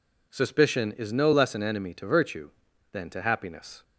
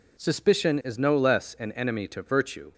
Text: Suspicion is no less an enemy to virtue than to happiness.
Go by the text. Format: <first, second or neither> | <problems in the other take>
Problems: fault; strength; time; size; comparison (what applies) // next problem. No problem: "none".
first | stops before "than to happiness"; at 2.7 s